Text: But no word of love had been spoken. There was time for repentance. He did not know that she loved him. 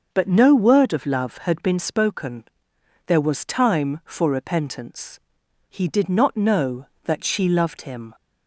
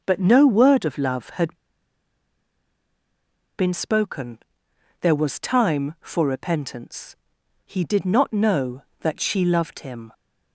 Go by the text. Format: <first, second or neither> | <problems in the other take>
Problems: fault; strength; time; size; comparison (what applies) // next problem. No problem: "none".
first | starts louder than the rest; until 1.0 s; 6.5 dB; also in the first // pauses between "had" and "been"; strong; at 1.5 s; 2.0 s long